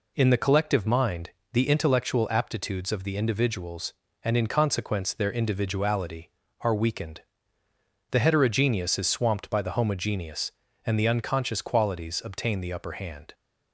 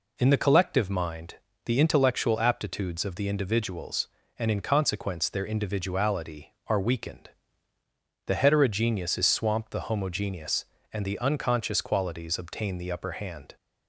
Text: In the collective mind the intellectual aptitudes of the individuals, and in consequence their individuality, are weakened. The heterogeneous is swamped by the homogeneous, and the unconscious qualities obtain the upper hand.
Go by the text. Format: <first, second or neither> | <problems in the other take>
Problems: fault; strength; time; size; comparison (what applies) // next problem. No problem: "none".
first | pauses between "mind" and "the"; slight; at 1.3 s; 0.30 s long; slight in the first // skips "by"; at 9.7 s